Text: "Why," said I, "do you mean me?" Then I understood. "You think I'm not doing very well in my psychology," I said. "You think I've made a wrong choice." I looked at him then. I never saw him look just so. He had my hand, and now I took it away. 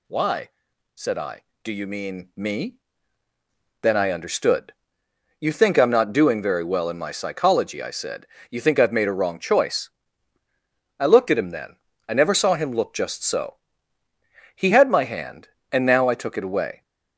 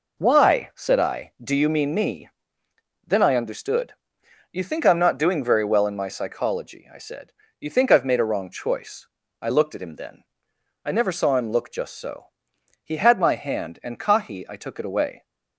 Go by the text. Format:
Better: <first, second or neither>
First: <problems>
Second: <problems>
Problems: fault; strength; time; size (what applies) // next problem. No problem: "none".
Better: first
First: none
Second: says "kahi" for "now"; at 13.9 s